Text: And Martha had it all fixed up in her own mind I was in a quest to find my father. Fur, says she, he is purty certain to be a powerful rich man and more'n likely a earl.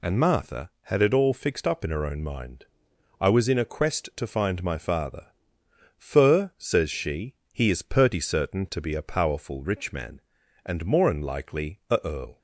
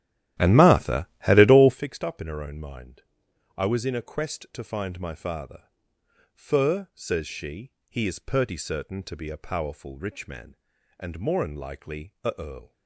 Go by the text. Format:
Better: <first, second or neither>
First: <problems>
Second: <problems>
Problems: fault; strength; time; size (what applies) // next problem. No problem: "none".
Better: first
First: pauses between "mind" and "I"; noticeable; at 2.6 s; 0.54 s long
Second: starts louder than the rest; strong; until 1.8 s; 12.5 dB // pauses between "mind" and "I"; noticeable; at 3.0 s; 0.54 s long